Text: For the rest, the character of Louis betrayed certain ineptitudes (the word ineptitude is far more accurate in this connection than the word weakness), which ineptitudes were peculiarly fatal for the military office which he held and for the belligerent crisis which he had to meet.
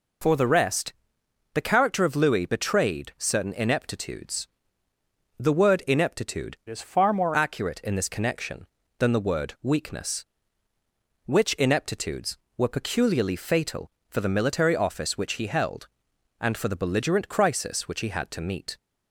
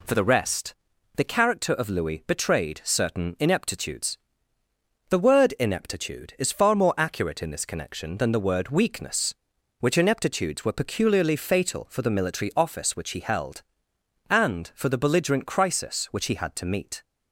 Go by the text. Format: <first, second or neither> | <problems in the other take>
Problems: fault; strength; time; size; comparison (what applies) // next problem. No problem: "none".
second | changes voice from "is" to "more"; from 6.6 to 7.3 s; 0.7 s long